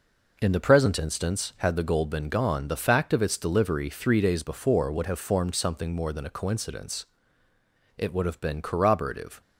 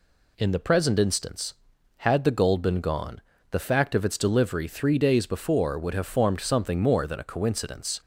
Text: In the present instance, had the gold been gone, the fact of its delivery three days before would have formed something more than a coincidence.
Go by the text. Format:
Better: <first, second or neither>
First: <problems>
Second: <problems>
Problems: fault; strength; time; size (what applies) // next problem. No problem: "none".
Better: second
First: goes on to say "It would have been corroborative"; from 7.9 s on; 1.4 s long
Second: none